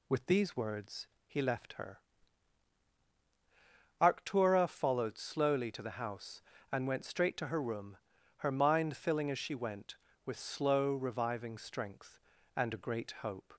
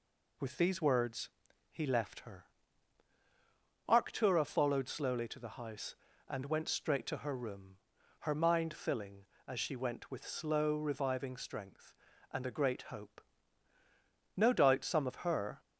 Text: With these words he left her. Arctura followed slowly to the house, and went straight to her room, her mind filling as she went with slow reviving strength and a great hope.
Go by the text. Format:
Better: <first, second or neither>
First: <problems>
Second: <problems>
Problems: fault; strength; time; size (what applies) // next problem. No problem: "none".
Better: first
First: pauses between "words" and "he"; slight; at 1.0 s; 0.18 s long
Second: pauses between "words" and "he"; at 1.2 s; 0.42 s long // goes on to say "No doubt some of her"; noticeable; from 14.3 s on; 1.2 s long